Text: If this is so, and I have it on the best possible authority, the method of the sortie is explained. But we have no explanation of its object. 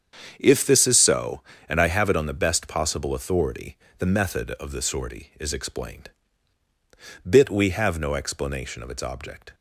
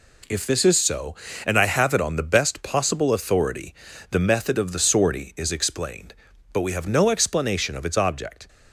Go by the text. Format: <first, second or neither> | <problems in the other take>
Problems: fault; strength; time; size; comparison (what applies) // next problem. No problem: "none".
second | starts louder than the rest; strong; until 1.3 s; 7.5 dB // says "Bit" for "But"; at 7.2 s